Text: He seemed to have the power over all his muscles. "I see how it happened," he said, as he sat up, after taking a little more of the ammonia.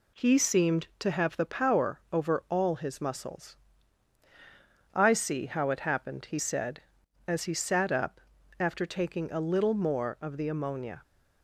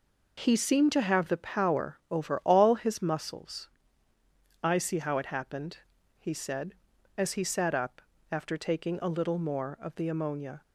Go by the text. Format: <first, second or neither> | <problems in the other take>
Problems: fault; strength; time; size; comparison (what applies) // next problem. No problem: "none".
neither | none